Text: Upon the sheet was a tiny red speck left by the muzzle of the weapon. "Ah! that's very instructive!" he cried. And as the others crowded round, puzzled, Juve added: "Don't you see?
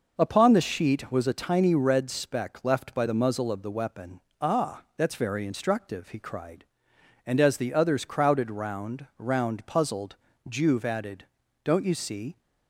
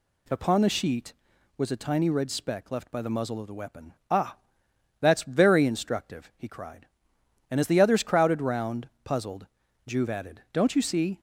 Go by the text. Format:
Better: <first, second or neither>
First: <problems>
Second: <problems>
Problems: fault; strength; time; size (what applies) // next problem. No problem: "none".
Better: second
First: says "round" twice; at 9.1 s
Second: none